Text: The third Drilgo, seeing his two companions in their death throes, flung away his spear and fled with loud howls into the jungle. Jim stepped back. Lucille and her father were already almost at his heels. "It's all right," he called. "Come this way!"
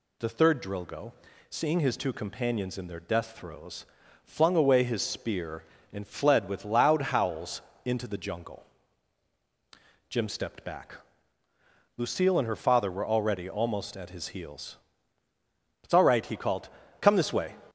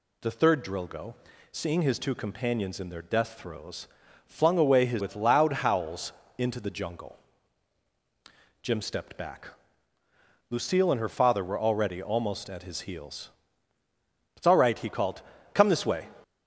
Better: first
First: pauses between "howls" and "into"; slight; at 7.6 s; 0.24 s long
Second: skips "spear and fled"; at 5.0 s // pauses between "howls" and "into"; slight; at 6.1 s; 0.26 s long

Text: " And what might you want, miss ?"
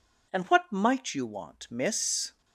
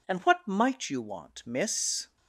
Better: neither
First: none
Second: none

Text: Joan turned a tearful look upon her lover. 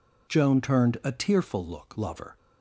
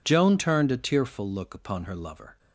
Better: second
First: skips "upon her"; at 1.9 s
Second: none

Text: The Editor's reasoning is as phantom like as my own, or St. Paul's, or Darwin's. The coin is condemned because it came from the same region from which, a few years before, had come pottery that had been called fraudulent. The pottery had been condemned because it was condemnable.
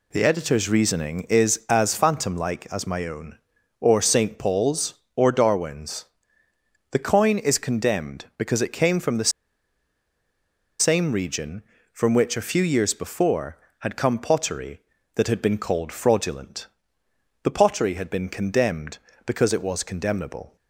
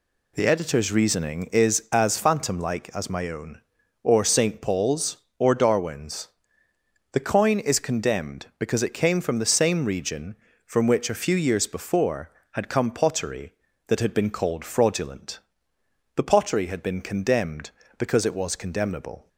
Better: second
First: pauses between "the" and "same"; strong; at 9.3 s; 1.5 s long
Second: none

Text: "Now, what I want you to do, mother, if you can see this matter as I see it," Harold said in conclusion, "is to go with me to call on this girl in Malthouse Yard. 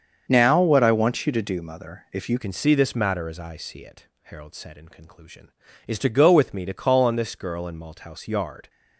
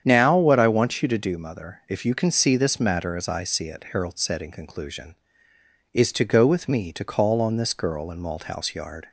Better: second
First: starts louder than the rest; until 1.3 s; 7 dB // changes voice at "can"; from 2.3 s on; 6.3 s long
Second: starts louder than the rest; strong; until 1.0 s; 8.5 dB

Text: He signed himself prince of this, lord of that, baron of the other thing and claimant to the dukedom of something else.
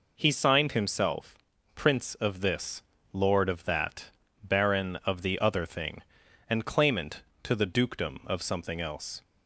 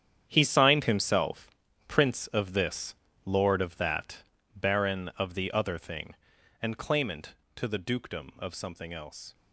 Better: first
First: pauses between "himself" and "prince"; at 1.3 s; 0.40 s long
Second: gets quieter; strong; throughout; 12.5 dB // pauses between "himself" and "prince"; at 1.4 s; 0.40 s long

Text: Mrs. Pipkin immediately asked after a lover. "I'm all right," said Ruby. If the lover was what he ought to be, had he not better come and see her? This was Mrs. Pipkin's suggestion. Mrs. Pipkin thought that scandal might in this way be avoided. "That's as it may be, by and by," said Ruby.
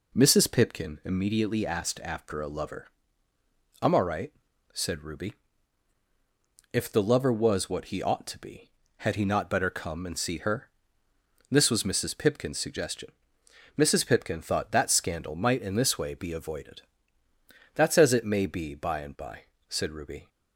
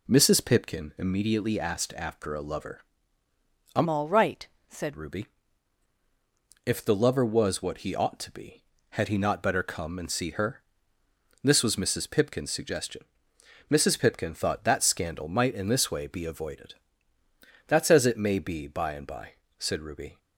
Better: first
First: none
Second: changes voice from "all" to "said"; from 3.8 to 4.9 s; 1.1 s long

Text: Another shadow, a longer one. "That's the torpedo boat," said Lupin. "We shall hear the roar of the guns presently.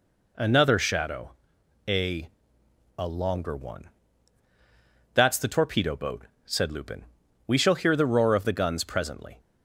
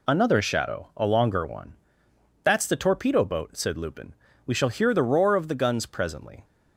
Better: second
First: says "a" twice; at 2.9 s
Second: none

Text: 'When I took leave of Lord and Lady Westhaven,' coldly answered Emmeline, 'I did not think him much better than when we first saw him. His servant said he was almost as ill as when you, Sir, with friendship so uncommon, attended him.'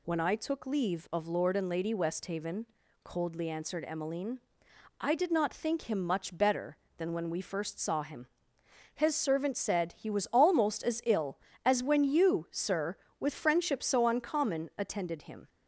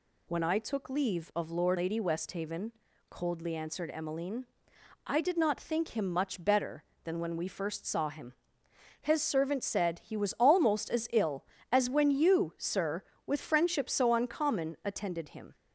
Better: first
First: none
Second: skips "and"; at 1.7 s

